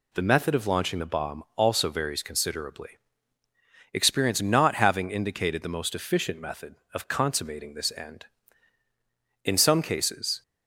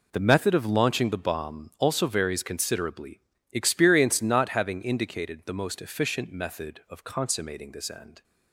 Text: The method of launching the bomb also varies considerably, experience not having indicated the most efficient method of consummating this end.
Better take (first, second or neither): second